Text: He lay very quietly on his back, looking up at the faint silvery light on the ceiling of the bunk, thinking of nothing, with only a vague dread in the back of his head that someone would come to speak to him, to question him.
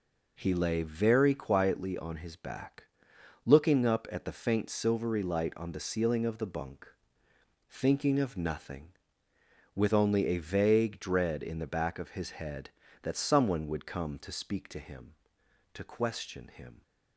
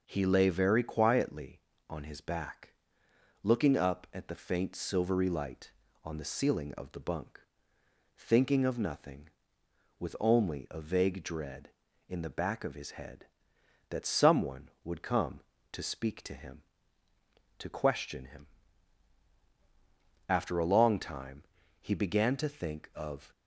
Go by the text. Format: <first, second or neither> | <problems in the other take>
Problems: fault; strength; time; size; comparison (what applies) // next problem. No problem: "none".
first | goes on to say "After a long time he began to think of"; strong; from 20.2 s on; 3.0 s long